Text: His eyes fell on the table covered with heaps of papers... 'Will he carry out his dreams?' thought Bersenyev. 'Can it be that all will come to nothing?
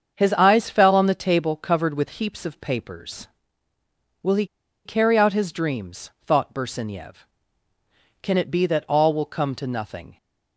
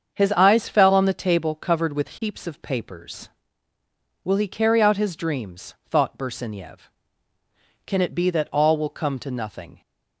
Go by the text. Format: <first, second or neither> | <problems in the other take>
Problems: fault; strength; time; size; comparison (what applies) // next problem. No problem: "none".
second | starts louder than the rest; until 1.1 s; 7 dB; also in the second // pauses between "he" and "carry"; at 4.4 s; 0.40 s long